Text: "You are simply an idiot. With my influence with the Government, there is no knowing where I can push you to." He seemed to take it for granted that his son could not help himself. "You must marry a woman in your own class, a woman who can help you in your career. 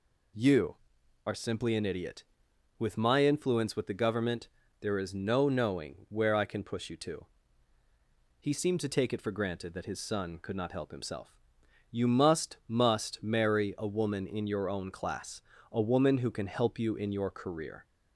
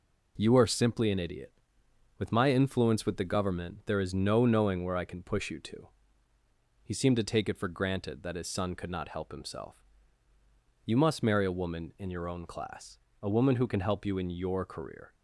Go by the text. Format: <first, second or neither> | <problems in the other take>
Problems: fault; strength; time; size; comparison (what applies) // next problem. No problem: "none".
second | says "must" twice; at 12.6 s